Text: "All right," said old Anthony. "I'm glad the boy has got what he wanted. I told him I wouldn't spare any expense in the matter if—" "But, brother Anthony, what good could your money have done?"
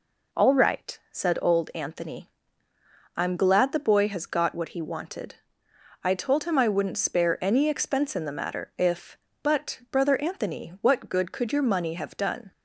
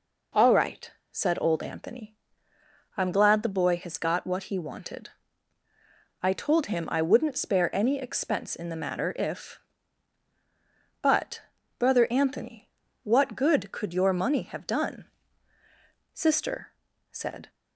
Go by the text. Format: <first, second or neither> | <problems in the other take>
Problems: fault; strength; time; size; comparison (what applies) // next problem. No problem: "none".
first | goes on to say "Sister said"; from 16.1 s on; 1.3 s long